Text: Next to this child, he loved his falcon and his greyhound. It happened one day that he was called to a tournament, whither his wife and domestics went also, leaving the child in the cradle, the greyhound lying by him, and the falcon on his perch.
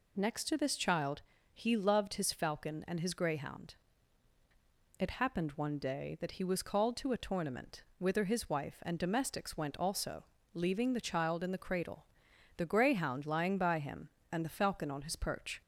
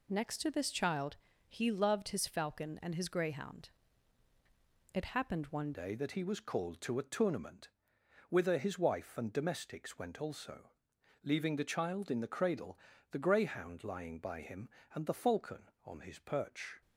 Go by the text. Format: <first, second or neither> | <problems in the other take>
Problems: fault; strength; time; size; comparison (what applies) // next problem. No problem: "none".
first | changes voice at "day"; from 5.7 s on; 11.1 s long